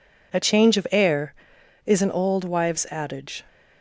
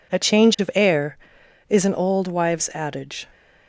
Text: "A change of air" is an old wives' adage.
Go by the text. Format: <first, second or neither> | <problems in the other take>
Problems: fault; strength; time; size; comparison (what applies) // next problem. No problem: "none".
neither | none